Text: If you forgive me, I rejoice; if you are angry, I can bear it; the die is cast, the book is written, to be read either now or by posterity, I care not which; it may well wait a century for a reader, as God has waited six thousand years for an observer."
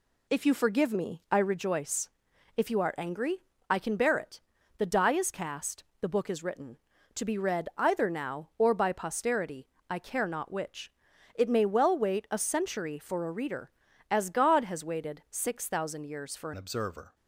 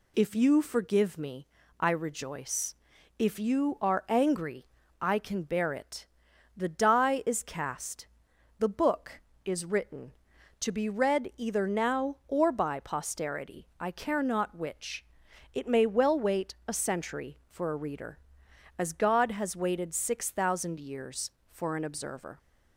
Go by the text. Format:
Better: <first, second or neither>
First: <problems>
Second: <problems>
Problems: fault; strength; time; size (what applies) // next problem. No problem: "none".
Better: second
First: changes voice at "an"; from 16.5 s on; 0.6 s long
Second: none